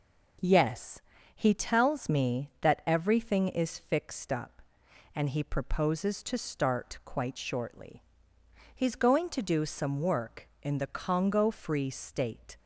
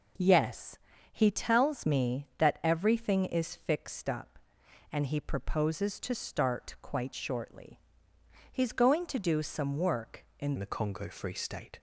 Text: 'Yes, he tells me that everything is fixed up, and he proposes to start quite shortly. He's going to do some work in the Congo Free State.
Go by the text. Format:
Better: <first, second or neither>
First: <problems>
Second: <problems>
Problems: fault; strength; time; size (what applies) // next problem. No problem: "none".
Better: first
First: none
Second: changes voice at "the"; from 10.5 s on; 1.2 s long